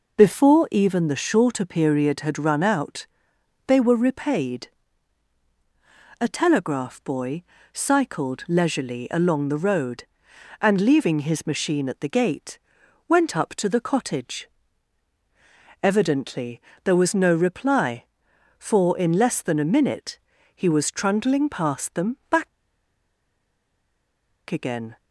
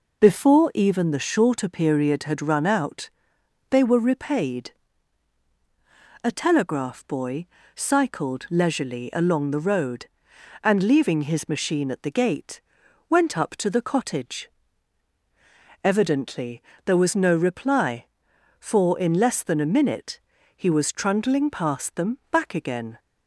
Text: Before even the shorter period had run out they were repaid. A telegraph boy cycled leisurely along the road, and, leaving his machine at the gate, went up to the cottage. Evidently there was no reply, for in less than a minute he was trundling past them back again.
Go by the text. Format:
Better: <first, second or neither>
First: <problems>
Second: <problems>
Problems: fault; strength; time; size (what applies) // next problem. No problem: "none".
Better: second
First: pauses between "out" and "they"; noticeable; at 3.0 s; 0.62 s long // pauses between "boy" and "cycled"; slight; at 7.4 s; 0.28 s long // pauses between "Evidently" and "there"; slight; at 16.5 s; 0.24 s long // pauses between "minute" and "he"; slight; at 20.1 s; 0.36 s long // pauses between "back" and "again"; strong; at 22.4 s; 2.0 s long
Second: pauses between "out" and "they"; noticeable; at 3.0 s; 0.62 s long // pauses between "boy" and "cycled"; slight; at 7.4 s; 0.28 s long // pauses between "Evidently" and "there"; slight; at 16.6 s; 0.24 s long // pauses between "minute" and "he"; slight; at 20.1 s; 0.36 s long